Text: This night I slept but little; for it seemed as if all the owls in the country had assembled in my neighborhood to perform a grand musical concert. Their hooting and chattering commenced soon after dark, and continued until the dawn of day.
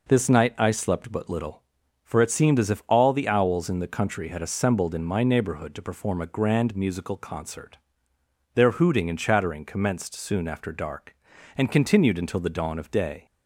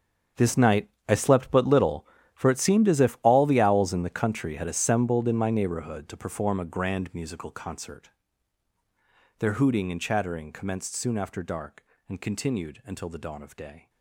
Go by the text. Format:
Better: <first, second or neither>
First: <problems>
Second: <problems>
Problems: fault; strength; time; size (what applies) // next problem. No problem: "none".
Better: first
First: none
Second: gets quieter; strong; throughout; 15 dB // pauses between "night" and "I"; slight; at 0.8 s; 0.18 s long